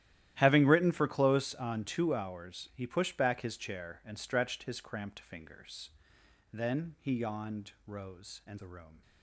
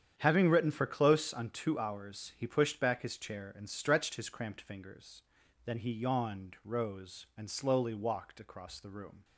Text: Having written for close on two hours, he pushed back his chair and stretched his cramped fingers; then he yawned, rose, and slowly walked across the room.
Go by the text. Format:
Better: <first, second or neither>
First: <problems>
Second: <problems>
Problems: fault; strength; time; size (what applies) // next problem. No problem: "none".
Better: second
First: starts louder than the rest; strong; until 1.3 s; 13 dB // skips "slowly walked across"; at 8.5 s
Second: starts louder than the rest; strong; until 1.1 s; 8.5 dB